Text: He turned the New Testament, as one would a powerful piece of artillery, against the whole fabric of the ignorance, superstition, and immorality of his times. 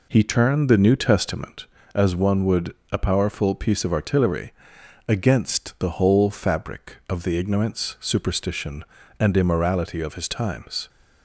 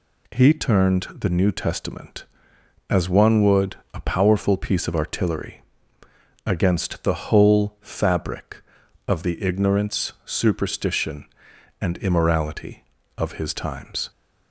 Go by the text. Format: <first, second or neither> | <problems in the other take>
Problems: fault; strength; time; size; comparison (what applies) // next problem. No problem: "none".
second | starts louder than the rest; until 1.9 s; 3.5 dB // pauses between "would" and "a"; slight; at 2.7 s; 0.16 s long; slight in the second